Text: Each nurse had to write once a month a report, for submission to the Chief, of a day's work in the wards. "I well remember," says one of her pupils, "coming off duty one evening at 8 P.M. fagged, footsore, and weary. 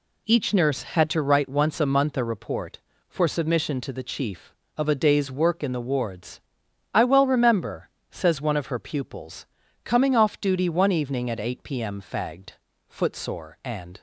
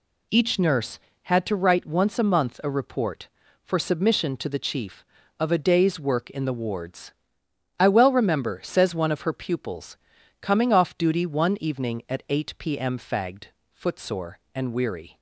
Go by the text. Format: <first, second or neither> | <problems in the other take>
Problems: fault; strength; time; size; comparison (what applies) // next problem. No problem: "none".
second | stops before "weary"; at 13.9 s